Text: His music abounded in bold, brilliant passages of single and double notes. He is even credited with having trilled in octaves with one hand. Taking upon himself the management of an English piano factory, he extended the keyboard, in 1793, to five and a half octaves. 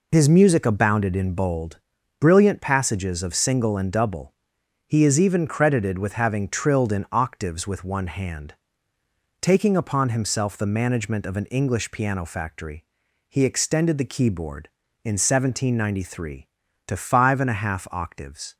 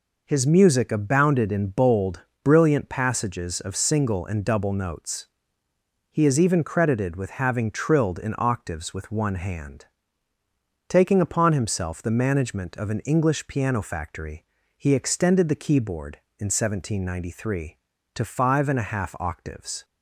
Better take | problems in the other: second | skips "notes"; at 4.6 s

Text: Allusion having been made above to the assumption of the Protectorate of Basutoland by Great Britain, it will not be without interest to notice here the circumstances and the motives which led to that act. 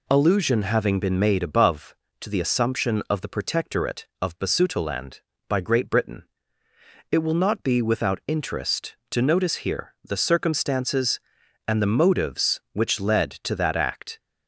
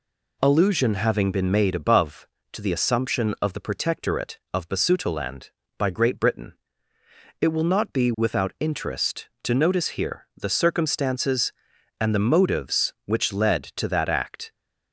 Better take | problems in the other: neither | none

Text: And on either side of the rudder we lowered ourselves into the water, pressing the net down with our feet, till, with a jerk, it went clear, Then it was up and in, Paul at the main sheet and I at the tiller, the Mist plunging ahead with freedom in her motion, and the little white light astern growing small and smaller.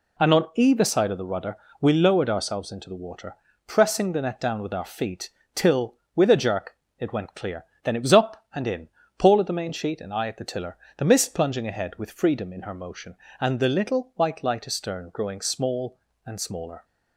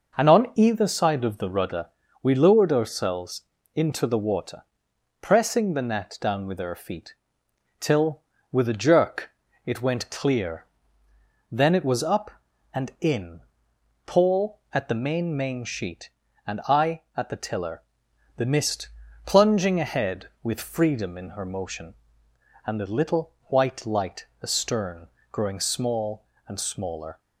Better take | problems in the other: first | pauses between "rudder" and "we"; slight; at 1.8 s; 0.32 s long; slight in the first // pauses between "ourselves" and "into"; slight; at 3.4 s; 0.32 s long // says "main" twice; at 15.3 s // pauses between "Mist" and "plunging"; slight; at 18.8 s; 0.36 s long // pauses between "light" and "astern"; slight; at 24.2 s; 0.16 s long // pauses between "astern" and "growing"; slight; at 25.0 s; 0.24 s long

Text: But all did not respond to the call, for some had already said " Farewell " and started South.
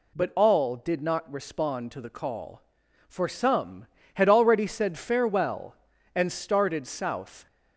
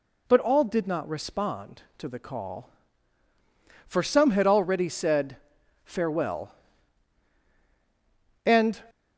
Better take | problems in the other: first | stops before "started South"; at 8.8 s

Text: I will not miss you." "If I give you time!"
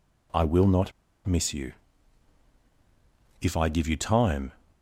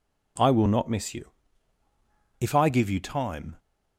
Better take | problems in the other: second | pauses between "not" and "miss"; slight; at 0.9 s; 0.33 s long

